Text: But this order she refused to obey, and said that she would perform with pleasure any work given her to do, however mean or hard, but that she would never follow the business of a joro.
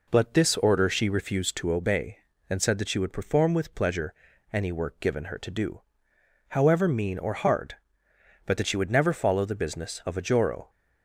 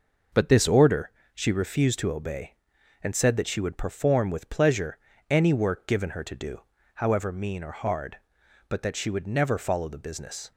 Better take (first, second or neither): first